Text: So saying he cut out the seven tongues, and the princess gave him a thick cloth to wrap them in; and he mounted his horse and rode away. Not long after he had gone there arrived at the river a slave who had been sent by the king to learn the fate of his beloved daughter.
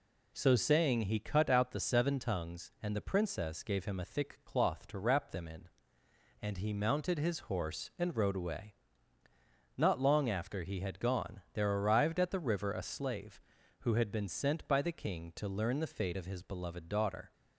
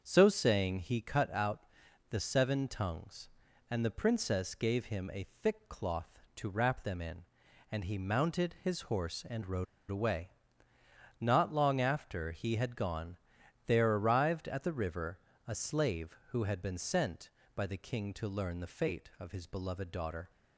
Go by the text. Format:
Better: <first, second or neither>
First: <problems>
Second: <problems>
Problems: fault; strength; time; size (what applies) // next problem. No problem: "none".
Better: first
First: none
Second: starts louder than the rest; until 1.0 s; 7 dB // pauses between "out" and "the"; at 1.6 s; 0.44 s long // pauses between "rode" and "away"; slight; at 9.6 s; 0.24 s long // pauses between "gone" and "there"; noticeable; at 13.1 s; 0.50 s long // pauses between "river" and "a"; slight; at 15.1 s; 0.28 s long